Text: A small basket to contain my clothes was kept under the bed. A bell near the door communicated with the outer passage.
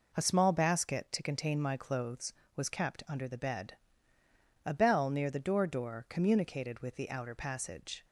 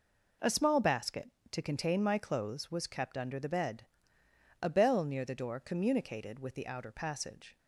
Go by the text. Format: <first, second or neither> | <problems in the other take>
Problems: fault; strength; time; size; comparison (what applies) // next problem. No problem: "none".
second | says "door" twice; at 5.6 s